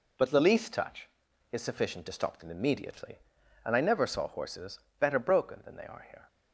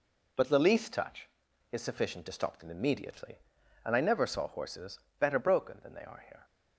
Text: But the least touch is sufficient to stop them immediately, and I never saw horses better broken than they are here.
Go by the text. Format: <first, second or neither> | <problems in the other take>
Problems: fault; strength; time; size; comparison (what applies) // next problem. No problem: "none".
neither | pauses between "horses" and "better"; slight; the same in both